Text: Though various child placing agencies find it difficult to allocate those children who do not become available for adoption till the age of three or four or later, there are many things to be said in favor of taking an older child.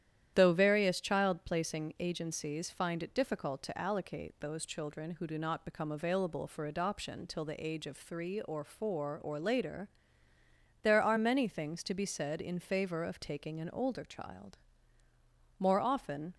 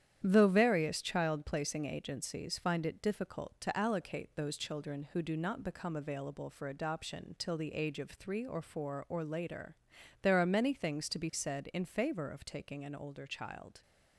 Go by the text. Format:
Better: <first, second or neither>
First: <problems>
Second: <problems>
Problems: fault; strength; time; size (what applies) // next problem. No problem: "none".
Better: second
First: starts louder than the rest; strong; until 1.3 s; 11 dB // goes on to say "More often"; noticeable; from 15.5 s on; 0.76 s long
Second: starts louder than the rest; strong; until 1.2 s; 10 dB